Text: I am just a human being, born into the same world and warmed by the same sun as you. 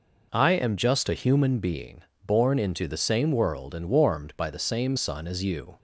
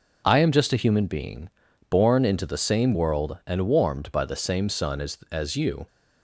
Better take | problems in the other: first | says "as" twice; at 5.3 s

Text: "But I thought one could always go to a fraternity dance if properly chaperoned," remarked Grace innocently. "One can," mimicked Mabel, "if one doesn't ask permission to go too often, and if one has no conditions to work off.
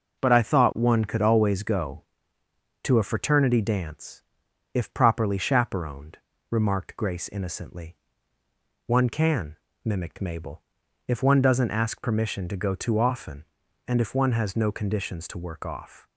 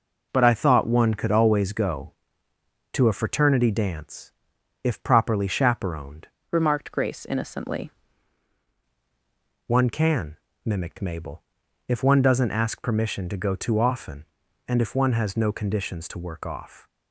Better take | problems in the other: first | pauses between "dance" and "if"; noticeable; at 4.3 s; 0.52 s long; noticeable in the first // changes voice from "remarked" to "innocently"; from 6.5 to 7.8 s; 1.3 s long

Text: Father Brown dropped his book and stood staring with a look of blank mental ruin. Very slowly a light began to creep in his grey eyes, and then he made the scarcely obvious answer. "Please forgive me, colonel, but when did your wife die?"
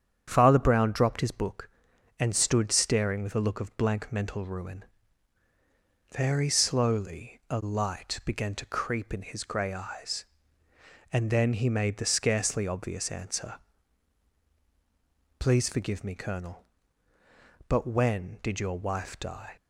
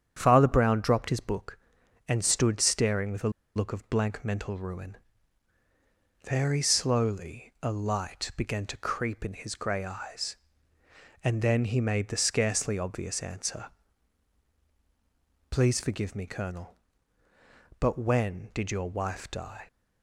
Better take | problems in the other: first | starts louder than the rest; strong; until 1.1 s; 8.5 dB; strong in the first // pauses between "a" and "look"; slight; at 3.2 s; 0.26 s long

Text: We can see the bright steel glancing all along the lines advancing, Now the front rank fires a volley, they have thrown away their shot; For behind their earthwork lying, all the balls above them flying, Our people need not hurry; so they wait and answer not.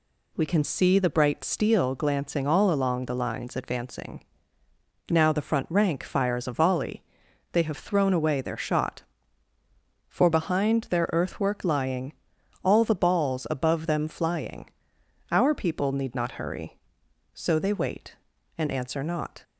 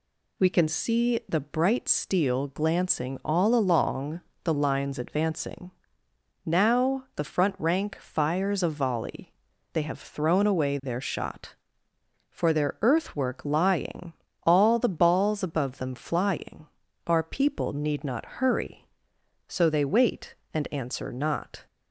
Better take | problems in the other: first | pauses between "along" and "the"; slight; at 4.2 s; 0.22 s long // skips "behind"; at 12.5 s

